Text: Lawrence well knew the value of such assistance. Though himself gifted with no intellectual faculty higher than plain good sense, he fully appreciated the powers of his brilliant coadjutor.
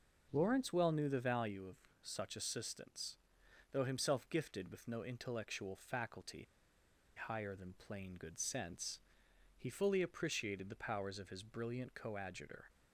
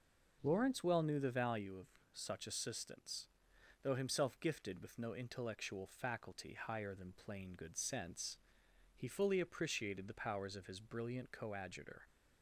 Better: second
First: pauses between "of" and "such"; slight; at 1.7 s; 0.26 s long // pauses between "faculty" and "higher"; noticeable; at 6.4 s; 0.72 s long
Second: pauses between "of" and "such"; slight; at 1.8 s; 0.26 s long

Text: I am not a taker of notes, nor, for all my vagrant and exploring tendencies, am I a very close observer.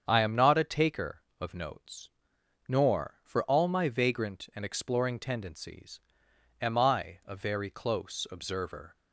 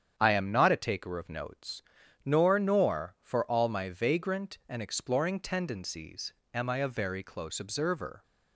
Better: first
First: starts louder than the rest; strong; until 1.0 s; 7.5 dB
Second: starts louder than the rest; strong; until 1.1 s; 8.5 dB // says "nor" twice; at 2.5 s

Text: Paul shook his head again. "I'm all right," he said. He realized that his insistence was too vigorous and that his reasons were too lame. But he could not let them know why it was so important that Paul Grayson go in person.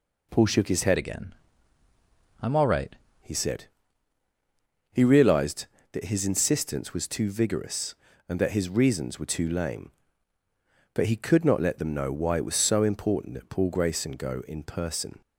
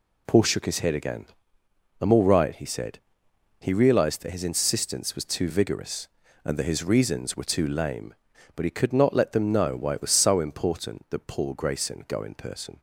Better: second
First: changes voice from "again" to "right"; from 0.9 to 2.9 s; 2.0 s long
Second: none

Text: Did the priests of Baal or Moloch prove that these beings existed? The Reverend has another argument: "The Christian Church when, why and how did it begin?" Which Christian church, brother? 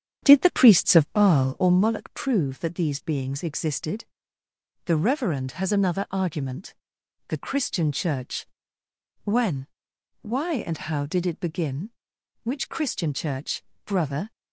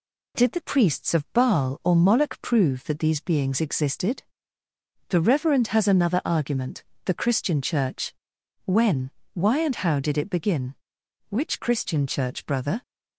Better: second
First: starts louder than the rest; strong; until 1.7 s; 8.5 dB // pauses between "Church" and "when"; noticeable; at 8.4 s; 0.78 s long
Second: pauses between "Church" and "when"; noticeable; at 8.1 s; 0.52 s long

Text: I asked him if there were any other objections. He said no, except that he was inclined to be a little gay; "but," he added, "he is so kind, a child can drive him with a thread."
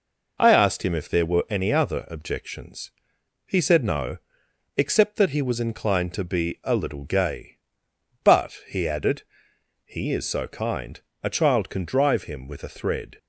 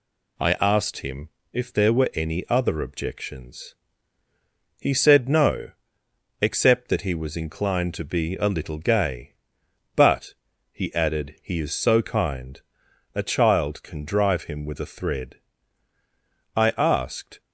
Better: first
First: none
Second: pauses between "him" and "if"; slight; at 1.2 s; 0.24 s long // goes on to say "I asked"; noticeable; from 16.5 s on; 0.84 s long

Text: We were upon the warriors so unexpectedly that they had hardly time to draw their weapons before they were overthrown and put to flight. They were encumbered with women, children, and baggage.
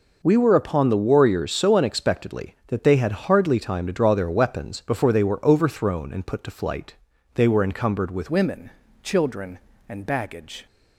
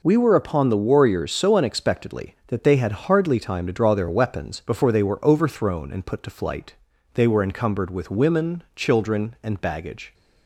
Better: second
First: changes voice at "women"; from 8.2 s on; 2.4 s long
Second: none

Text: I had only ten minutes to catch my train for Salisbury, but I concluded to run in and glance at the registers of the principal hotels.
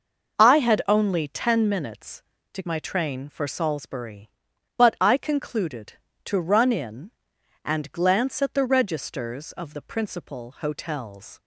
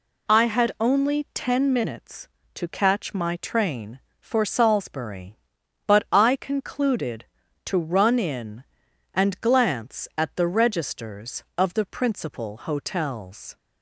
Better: second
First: skips "catch"; at 2.6 s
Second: none

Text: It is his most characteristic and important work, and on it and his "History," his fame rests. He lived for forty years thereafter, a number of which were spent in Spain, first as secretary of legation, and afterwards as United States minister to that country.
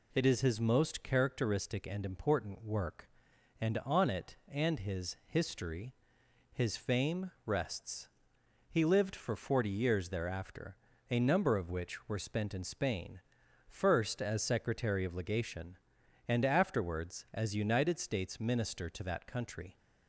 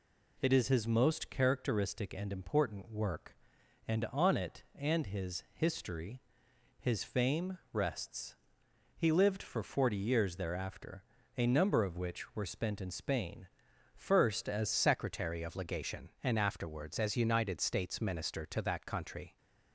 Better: first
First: none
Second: changes voice at "secretary"; from 14.7 s on; 4.6 s long

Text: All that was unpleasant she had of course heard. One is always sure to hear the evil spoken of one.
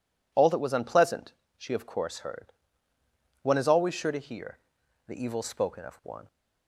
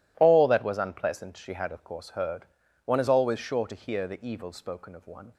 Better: second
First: pauses between "unpleasant" and "she"; slight; at 1.3 s; 0.26 s long // skips "had"; at 1.7 s // pauses between "hear" and "the"; noticeable; at 4.5 s; 0.50 s long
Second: none

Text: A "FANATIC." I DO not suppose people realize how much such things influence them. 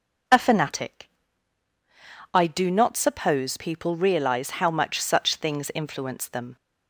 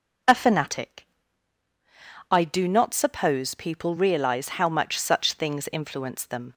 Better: neither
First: none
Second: none

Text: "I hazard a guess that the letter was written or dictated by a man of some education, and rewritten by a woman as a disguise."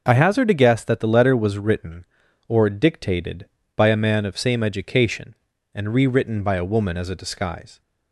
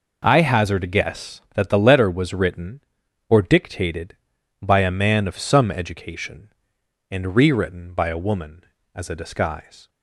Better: second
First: says "same" for "some"; at 4.3 s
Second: none

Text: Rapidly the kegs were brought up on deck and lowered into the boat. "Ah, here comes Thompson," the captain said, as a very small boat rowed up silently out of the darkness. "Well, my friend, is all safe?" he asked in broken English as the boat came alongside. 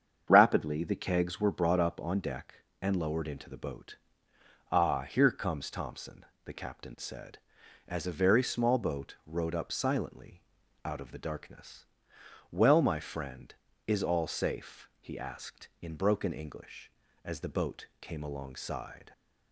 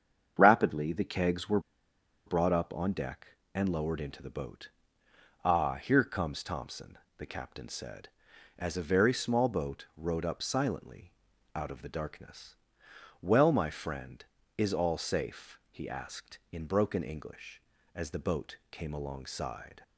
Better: first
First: starts louder than the rest; strong; until 1.2 s; 7.5 dB // pauses between "silently" and "out"; at 10.4 s; 0.44 s long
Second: starts louder than the rest; strong; until 1.3 s; 7.5 dB // pauses between "were" and "brought"; noticeable; at 1.5 s; 0.66 s long // pauses between "silently" and "out"; at 11.1 s; 0.44 s long

